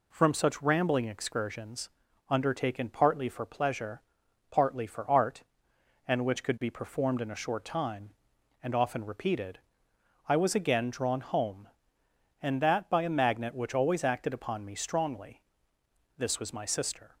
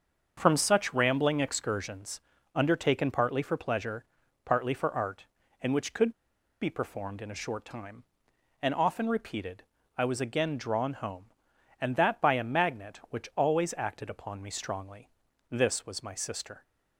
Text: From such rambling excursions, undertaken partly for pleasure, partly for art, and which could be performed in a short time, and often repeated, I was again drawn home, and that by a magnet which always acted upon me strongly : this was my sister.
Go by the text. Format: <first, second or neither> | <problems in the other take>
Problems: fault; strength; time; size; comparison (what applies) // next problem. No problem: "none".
first | starts louder than the rest; until 1.3 s; 6.5 dB // pauses between "could" and "be"; noticeable; at 6.1 s; 0.48 s long